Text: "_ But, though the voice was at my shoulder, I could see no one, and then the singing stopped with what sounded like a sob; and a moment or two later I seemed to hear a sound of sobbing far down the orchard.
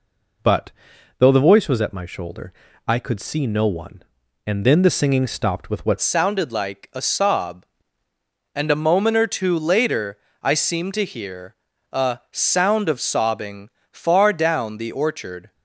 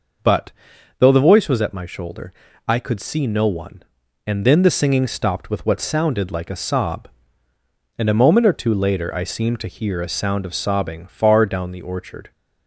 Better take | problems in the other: second | changes voice at "sounded"; from 5.9 s on; 9.6 s long // pauses between "later" and "I"; slight; at 10.1 s; 0.24 s long // pauses between "hear" and "a"; at 11.5 s; 0.38 s long // pauses between "sobbing" and "far"; slight; at 13.6 s; 0.22 s long

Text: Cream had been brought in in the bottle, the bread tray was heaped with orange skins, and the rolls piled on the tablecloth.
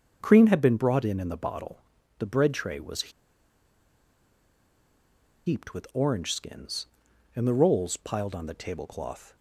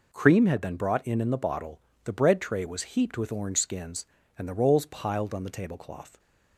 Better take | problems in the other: second | starts louder than the rest; until 1.2 s; 6.5 dB // pauses between "was" and "heaped"; strong; at 3.0 s; 2.3 s long

